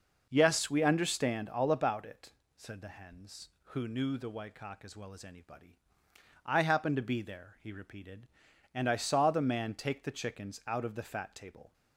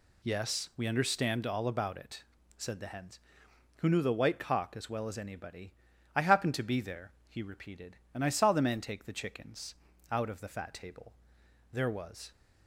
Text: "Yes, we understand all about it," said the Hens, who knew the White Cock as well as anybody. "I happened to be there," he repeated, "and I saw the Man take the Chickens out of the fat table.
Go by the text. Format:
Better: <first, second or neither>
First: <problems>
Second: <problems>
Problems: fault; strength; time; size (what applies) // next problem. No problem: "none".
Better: first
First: none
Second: pauses between "Chickens" and "out"; slight; at 9.7 s; 0.34 s long // goes on to say "There was"; from 11.7 s on; 0.58 s long